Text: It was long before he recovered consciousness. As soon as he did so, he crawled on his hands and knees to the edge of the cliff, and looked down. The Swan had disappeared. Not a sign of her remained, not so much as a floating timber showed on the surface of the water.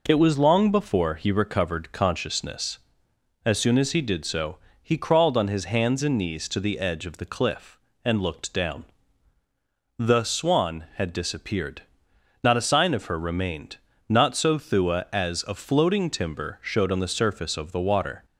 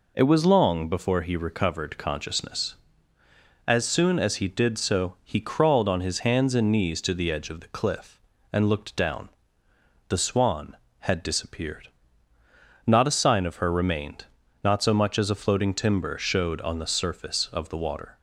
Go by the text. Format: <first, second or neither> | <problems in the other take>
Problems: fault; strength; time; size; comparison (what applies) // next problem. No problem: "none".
second | says "thua" for "much"; at 14.5 s